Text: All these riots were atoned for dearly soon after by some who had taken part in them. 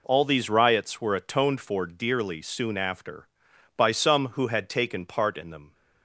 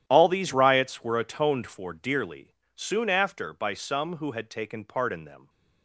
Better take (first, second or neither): first